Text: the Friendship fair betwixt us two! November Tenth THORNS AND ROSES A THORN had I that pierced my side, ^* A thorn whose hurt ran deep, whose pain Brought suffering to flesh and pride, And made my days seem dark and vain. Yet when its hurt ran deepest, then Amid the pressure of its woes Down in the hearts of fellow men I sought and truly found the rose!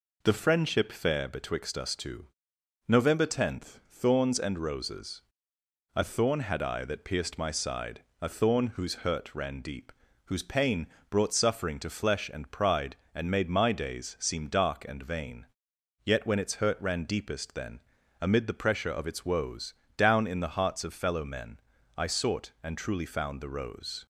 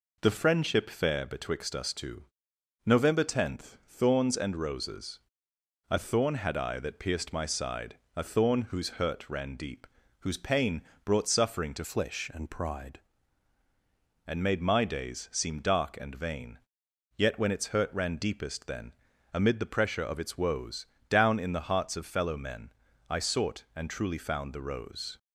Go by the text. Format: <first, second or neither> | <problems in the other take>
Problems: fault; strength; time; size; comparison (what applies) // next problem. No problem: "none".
first | pauses between "ROSES" and "A"; noticeable; at 5.2 s; 0.72 s long; noticeable in the first // pauses between "pain" and "Brought"; slight; at 10.8 s; 0.22 s long; slight in the first // changes voice from "flesh" to "pride"; from 11.8 to 12.9 s; 1.1 s long // pauses between "then" and "Amid"; at 18.9 s; 0.42 s long; also in the first // pauses between "woes" and "Down"; slight; at 20.8 s; 0.24 s long; slight in the first // pauses between "men" and "I"; at 22.7 s; 0.38 s long; also in the first